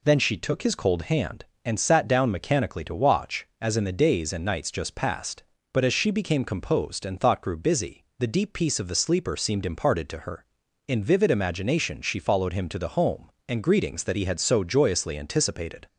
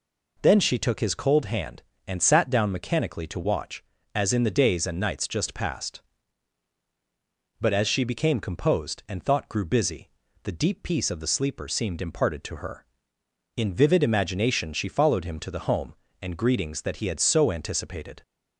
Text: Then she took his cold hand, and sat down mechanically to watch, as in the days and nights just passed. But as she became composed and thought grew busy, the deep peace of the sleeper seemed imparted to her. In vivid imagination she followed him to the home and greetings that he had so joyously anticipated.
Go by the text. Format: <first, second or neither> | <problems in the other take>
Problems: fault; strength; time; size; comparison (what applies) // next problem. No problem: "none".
first | skips "joyously"; at 17.4 s